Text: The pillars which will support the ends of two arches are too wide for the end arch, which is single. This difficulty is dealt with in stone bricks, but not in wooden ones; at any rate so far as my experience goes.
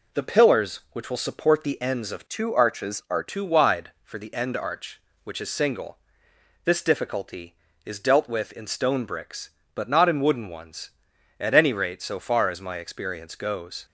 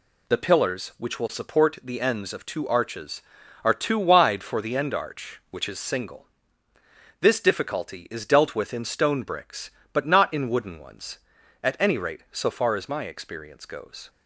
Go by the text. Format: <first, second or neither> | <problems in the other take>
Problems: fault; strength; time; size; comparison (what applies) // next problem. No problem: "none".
second | changes voice from "two" to "are"; from 2.2 to 3.2 s; 1.0 s long